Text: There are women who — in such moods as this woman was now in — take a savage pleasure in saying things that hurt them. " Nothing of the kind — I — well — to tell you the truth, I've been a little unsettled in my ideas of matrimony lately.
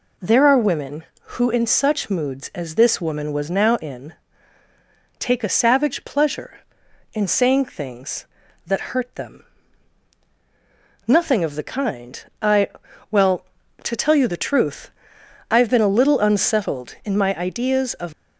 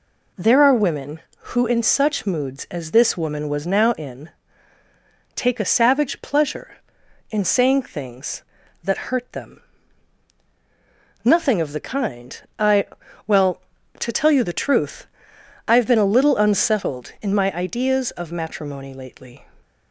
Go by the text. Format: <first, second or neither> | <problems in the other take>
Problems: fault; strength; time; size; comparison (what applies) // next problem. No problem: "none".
second | stops before "matrimony lately"; at 18.1 s